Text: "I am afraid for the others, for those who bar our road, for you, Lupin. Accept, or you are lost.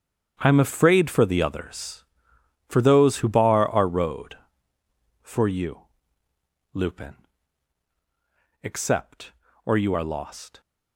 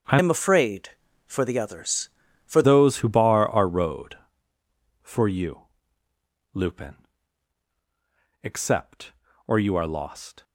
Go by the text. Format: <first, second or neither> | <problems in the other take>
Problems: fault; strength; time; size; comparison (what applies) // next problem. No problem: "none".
first | starts louder than the rest; until 1.4 s; 7 dB; strong in the first // changes voice from "am" to "for"; from 0.1 to 2.6 s; 2.5 s long